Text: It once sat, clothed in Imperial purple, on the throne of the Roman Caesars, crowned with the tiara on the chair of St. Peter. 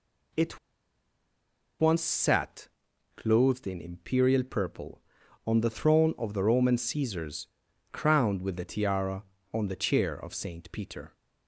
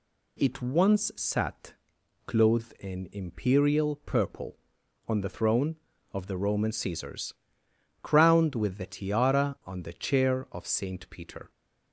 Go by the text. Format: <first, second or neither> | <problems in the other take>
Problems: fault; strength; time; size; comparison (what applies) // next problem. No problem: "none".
second | pauses between "It" and "once"; at 0.5 s; 1.2 s long